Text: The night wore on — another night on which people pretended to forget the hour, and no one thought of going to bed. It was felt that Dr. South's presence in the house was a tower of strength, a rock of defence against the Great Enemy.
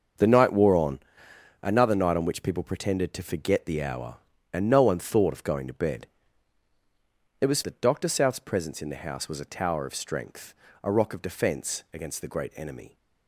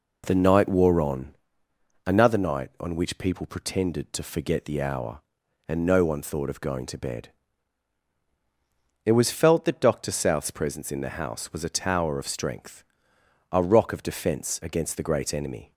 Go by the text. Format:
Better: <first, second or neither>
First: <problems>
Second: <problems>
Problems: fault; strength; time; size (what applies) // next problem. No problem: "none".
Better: second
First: starts louder than the rest; until 1.7 s; 6 dB // skips "felt"; at 7.6 s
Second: none